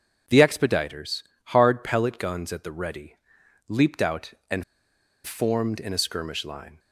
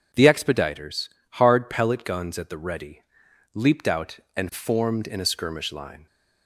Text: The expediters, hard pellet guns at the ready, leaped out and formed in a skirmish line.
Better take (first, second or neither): second